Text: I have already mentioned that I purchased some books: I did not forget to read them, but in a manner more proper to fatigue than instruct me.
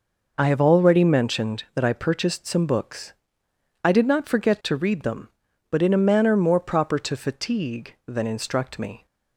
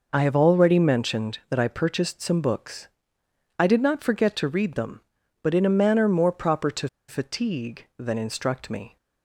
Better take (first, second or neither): first